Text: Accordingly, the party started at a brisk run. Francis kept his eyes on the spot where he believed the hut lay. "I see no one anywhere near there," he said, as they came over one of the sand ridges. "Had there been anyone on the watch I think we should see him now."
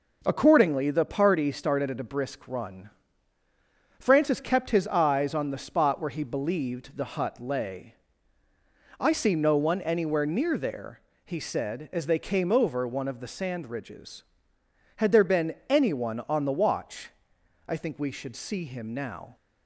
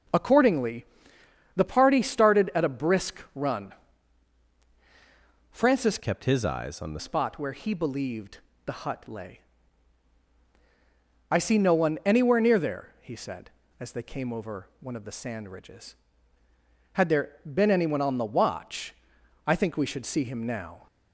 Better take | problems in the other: first | changes voice from "kept" to "the"; from 5.9 to 6.9 s; 1.0 s long // pauses between "believed" and "the"; slight; at 8.3 s; 0.26 s long // pauses between "watch" and "I"; noticeable; at 18.9 s; 0.52 s long; noticeable in the first

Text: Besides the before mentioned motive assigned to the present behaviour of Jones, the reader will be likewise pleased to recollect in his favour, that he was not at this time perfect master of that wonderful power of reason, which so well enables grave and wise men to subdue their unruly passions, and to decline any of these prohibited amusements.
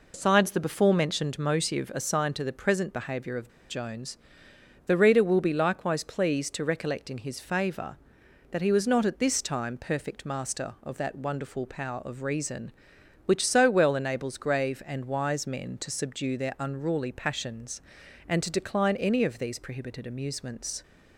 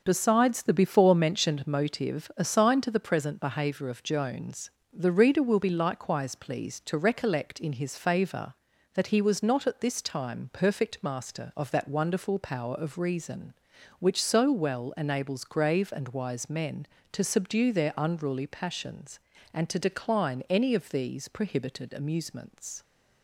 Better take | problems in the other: second | pauses between "of" and "Jones"; slight; at 3.4 s; 0.20 s long

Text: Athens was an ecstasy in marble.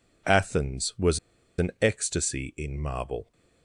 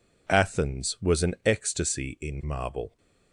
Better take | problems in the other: second | pauses between "was" and "an"; at 1.1 s; 0.39 s long

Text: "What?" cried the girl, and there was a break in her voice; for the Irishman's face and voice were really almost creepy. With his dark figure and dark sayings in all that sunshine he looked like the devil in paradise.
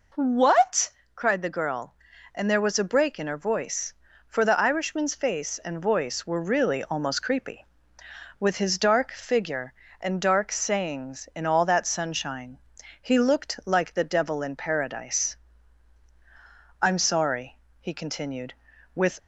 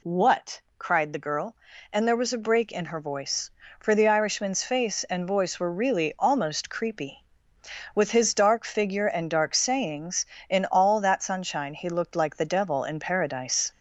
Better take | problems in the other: second | pauses between "sunshine" and "he"; at 12.5 s; 0.42 s long // goes on to say "I'm sorry he continued with"; strong; from 16.8 s on; 2.3 s long

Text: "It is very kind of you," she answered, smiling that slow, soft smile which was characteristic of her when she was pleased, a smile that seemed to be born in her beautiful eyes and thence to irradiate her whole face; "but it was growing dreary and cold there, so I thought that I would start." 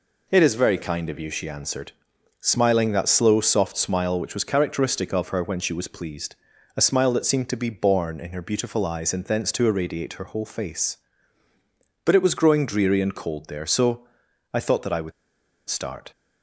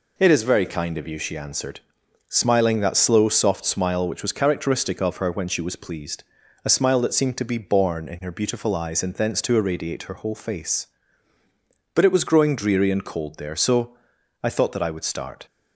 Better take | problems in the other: second | pauses between "so" and "I"; noticeable; at 14.0 s; 0.46 s long; noticeable in the second // pauses between "would" and "start"; noticeable; at 15.1 s; 0.57 s long

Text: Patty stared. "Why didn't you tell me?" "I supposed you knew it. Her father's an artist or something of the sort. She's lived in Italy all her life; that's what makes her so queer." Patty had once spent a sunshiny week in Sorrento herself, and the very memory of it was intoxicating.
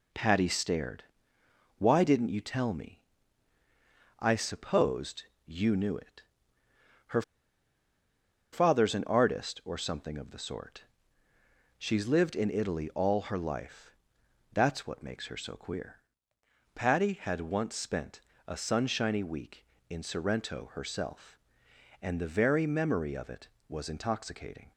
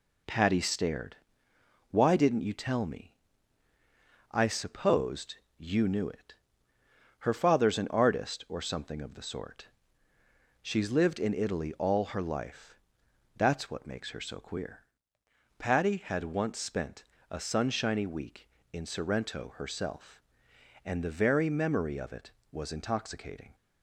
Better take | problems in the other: second | pauses between "supposed" and "you"; slight; at 5.2 s; 0.22 s long; slight in the second // pauses between "Her" and "father's"; strong; at 7.2 s; 1.3 s long // pauses between "spent" and "a"; slight; at 18.1 s; 0.26 s long; slight in the second

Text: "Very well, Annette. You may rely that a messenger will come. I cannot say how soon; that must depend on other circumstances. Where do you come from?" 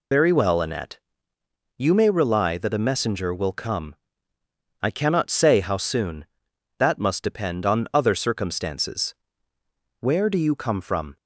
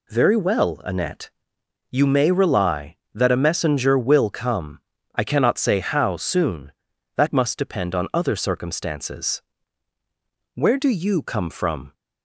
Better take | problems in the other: second | loses the start of "Very"; at 0.1 s; 70 ms

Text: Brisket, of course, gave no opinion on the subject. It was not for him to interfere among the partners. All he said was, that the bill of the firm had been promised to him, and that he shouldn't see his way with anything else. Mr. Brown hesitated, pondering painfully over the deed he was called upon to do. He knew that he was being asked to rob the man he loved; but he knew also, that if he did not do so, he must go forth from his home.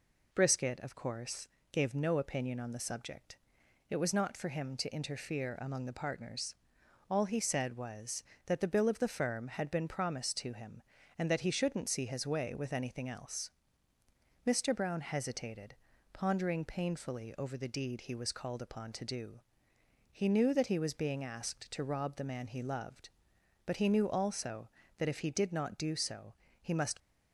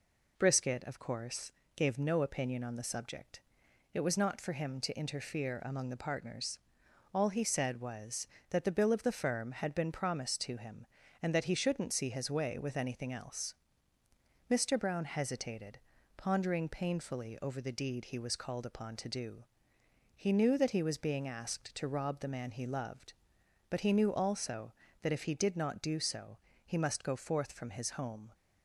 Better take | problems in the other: second | stops before "go forth from his home"; at 27.0 s

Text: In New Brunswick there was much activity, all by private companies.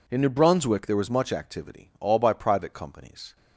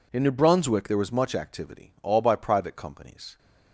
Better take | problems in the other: neither | none

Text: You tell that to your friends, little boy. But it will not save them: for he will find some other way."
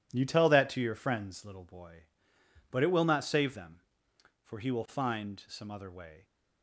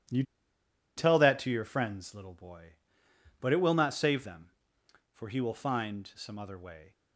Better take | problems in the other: first | pauses between "You" and "tell"; noticeable; at 0.2 s; 0.74 s long

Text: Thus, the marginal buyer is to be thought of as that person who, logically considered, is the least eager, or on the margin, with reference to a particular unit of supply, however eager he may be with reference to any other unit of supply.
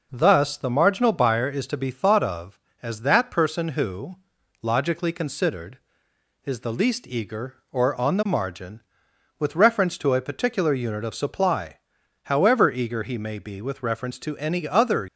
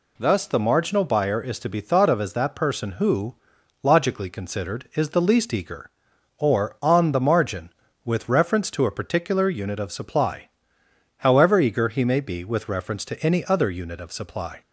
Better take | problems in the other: second | stops before "unit of supply"; at 15.0 s

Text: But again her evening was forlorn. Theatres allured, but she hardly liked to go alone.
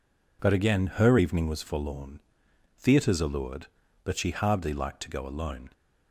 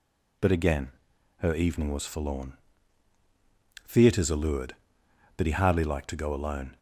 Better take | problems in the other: first | pauses between "again" and "her"; noticeable; at 0.9 s; 0.48 s long // says "he" for "she"; at 5.4 s

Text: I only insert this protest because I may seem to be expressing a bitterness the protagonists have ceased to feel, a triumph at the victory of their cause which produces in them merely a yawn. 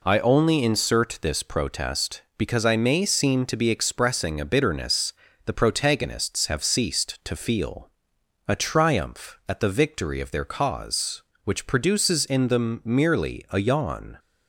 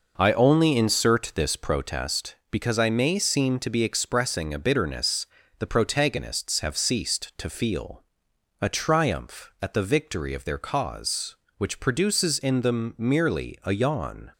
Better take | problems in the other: first | starts louder than the rest; noticeable; until 2.1 s; 5.5 dB // pauses between "bitterness" and "the"; slight; at 5.2 s; 0.32 s long; slight in the first

